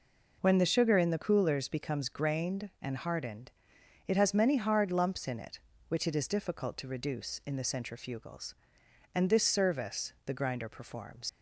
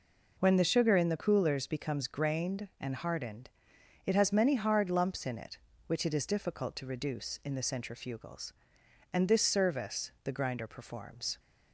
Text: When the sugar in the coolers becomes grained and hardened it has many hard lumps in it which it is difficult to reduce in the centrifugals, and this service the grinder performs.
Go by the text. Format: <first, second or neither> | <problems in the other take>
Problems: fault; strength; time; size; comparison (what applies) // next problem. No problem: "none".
second | pauses between "hardened" and "it"; noticeable; at 3.5 s; 0.56 s long; noticeable in the second // leaves "performs" unfinished; at 11.2 s; 110 ms